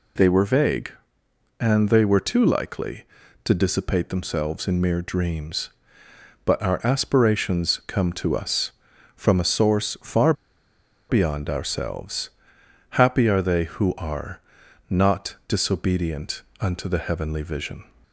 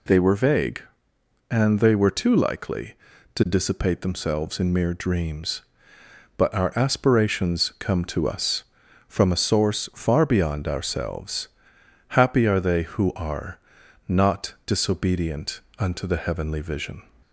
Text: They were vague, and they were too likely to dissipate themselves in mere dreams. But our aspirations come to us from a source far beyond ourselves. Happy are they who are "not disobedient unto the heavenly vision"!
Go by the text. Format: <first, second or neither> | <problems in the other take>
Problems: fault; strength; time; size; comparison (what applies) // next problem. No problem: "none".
second | pauses between "far" and "beyond"; noticeable; at 10.3 s; 0.76 s long // pauses between "are" and "not"; noticeable; at 14.4 s; 0.48 s long; noticeable in the second // pauses between "disobedient" and "unto"; slight; at 16.4 s; 0.18 s long; slight in the second